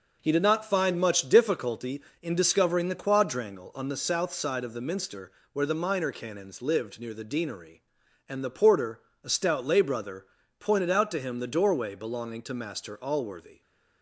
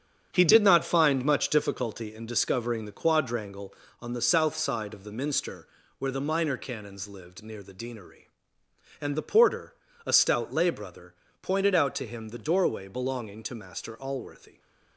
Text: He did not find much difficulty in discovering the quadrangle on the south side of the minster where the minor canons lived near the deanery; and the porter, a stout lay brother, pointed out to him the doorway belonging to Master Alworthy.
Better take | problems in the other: first | gets quieter; strong; throughout; 8 dB // pauses between "minster" and "where"; slight; at 5.6 s; 0.32 s long; slight in the first

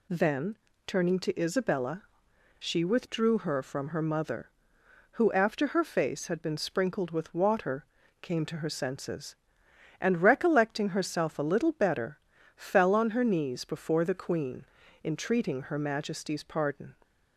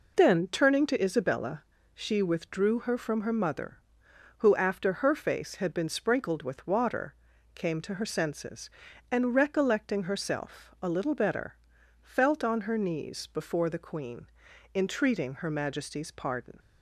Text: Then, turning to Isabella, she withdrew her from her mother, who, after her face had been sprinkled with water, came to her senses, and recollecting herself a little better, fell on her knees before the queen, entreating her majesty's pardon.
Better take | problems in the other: first | says "felt" for "fell"; at 12.0 s

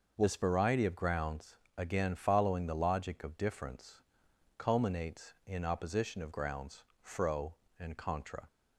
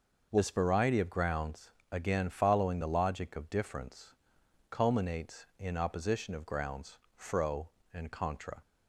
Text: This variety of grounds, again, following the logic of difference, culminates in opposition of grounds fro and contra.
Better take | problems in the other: neither | pauses between "grounds" and "fro"; slight; the same in both

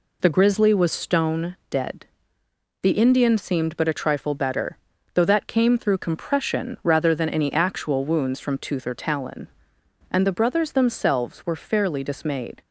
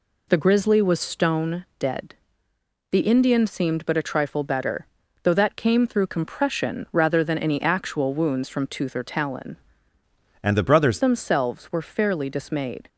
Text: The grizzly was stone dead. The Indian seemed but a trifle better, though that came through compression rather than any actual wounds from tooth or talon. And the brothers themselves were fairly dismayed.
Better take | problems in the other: first | changes voice from "And" to "brothers"; from 10.4 to 10.9 s; 0.5 s long

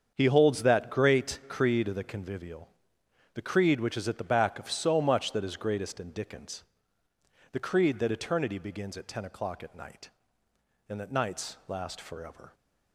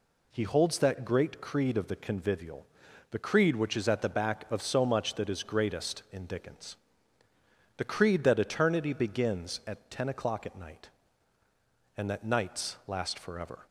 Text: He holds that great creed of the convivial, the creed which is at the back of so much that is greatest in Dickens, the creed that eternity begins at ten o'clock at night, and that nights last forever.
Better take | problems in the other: second | gets quieter; strong; throughout; 11 dB

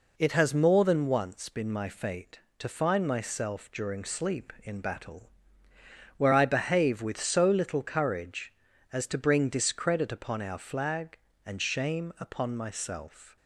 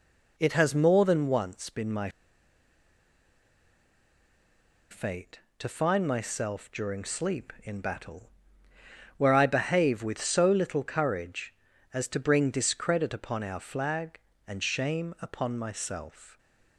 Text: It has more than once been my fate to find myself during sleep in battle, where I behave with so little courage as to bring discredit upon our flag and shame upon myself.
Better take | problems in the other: first | pauses between "my" and "fate"; strong; at 2.0 s; 2.8 s long

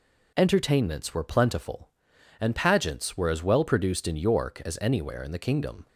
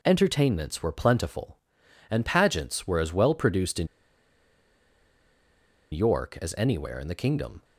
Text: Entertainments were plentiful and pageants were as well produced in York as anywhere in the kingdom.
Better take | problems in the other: first | pauses between "in" and "York"; strong; at 3.8 s; 2.0 s long

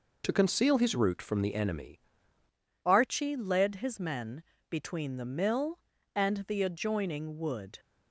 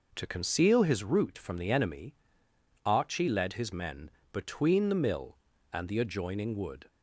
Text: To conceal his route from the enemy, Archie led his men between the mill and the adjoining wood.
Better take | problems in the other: second | changes voice at "Archie"; from 2.8 s on; 4.9 s long // pauses between "men" and "between"; slight; at 4.4 s; 0.30 s long; slight in the second

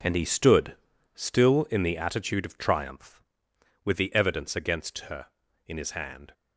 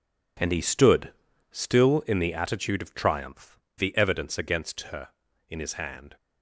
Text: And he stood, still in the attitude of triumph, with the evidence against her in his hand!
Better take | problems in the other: first | skips "with"; at 3.6 s

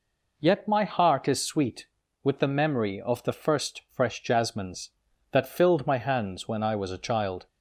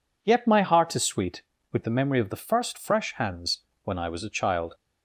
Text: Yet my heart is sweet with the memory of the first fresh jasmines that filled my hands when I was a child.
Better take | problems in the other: first | skips "jasmines that filled my"; at 3.1 s // pauses between "hands" and "when"; slight; at 3.5 s; 0.26 s long

